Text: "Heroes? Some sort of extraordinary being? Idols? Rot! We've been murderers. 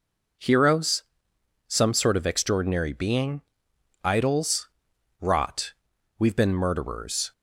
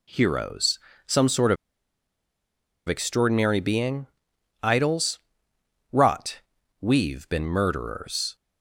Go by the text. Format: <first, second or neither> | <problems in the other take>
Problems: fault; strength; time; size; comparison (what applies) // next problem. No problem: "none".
first | pauses between "of" and "extraordinary"; strong; at 1.5 s; 1.3 s long